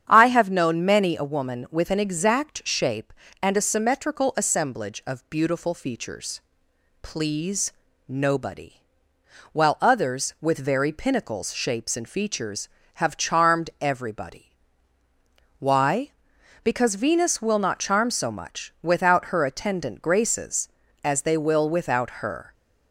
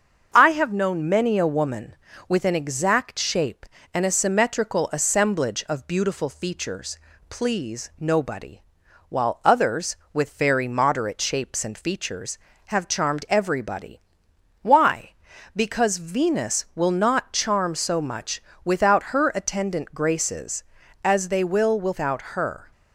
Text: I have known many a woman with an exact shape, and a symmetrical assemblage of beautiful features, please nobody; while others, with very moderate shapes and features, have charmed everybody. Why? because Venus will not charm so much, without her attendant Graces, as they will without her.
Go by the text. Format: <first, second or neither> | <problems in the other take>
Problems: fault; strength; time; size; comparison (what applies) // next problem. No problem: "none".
second | starts louder than the rest; strong; until 1.0 s; 8.5 dB; also in the second // pauses between "please" and "nobody"; slight; at 7.7 s; 0.36 s long // says "pinnacles" for "moderate"; at 10.9 s